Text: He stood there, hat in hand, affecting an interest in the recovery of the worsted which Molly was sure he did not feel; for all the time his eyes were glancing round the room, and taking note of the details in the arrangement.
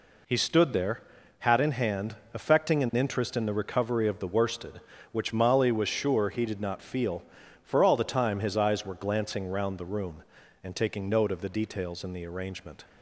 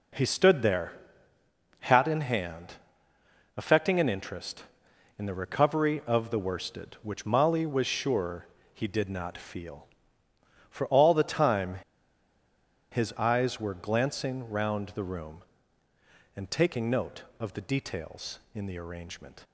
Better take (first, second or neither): first